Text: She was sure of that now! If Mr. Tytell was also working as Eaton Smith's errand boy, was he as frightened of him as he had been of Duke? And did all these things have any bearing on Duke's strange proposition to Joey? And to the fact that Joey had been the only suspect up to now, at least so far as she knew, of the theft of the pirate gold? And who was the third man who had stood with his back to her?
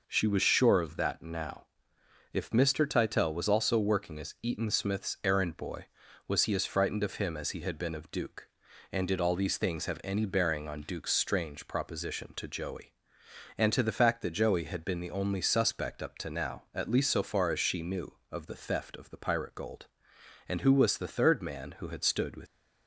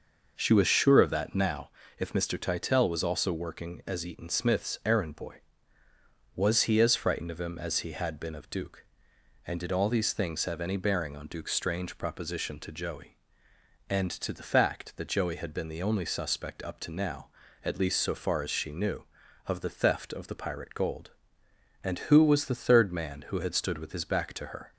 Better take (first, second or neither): second